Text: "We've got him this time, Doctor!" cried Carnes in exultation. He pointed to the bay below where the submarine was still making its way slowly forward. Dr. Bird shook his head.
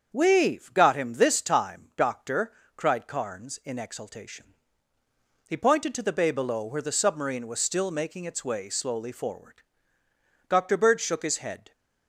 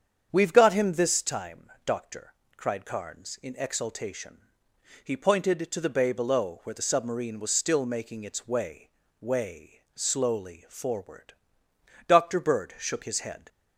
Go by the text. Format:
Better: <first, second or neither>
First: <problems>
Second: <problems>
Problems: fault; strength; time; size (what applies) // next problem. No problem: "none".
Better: first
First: starts louder than the rest; until 1.1 s; 7 dB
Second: starts louder than the rest; strong; until 1.3 s; 8 dB // says "way" twice; at 9.2 s